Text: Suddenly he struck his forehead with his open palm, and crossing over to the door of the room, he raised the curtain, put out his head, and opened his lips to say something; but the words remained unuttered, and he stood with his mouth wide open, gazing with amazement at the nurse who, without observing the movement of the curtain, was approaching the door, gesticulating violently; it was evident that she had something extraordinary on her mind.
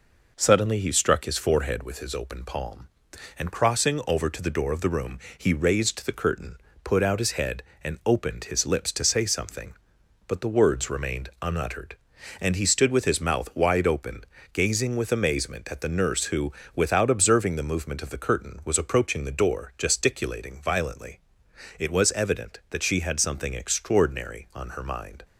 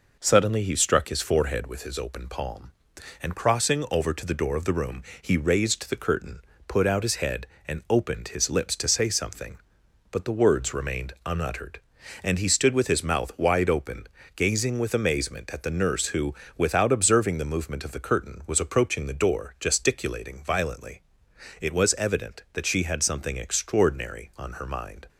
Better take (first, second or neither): neither